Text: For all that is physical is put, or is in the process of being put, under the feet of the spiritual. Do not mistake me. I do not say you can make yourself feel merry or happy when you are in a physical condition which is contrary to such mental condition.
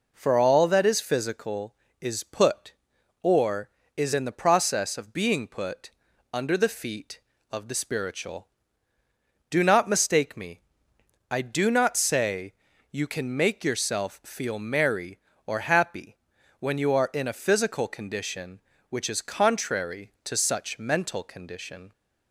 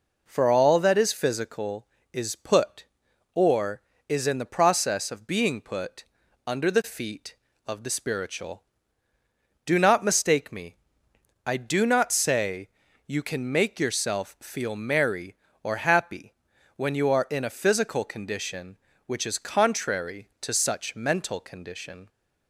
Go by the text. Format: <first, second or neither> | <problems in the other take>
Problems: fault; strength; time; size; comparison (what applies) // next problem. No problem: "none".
neither | pauses between "say" and "you"; the same in both // pauses between "happy" and "when"; the same in both